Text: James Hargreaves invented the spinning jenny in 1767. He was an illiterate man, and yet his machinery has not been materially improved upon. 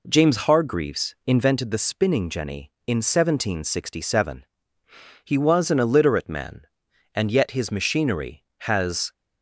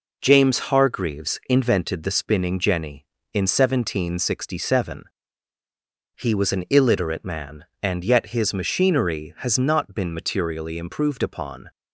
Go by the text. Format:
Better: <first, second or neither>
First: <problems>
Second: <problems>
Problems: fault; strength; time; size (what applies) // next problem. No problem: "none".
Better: second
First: stops before "not been materially improved upon"; at 9.1 s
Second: none